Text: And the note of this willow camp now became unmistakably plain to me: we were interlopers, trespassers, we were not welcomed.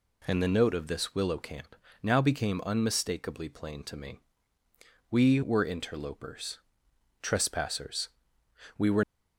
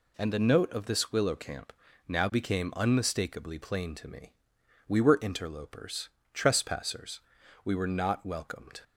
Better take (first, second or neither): second